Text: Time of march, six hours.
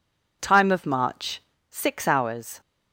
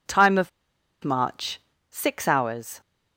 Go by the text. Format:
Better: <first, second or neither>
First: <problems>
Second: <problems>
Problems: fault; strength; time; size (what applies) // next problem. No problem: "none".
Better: first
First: none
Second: pauses between "of" and "march"; noticeable; at 0.4 s; 0.54 s long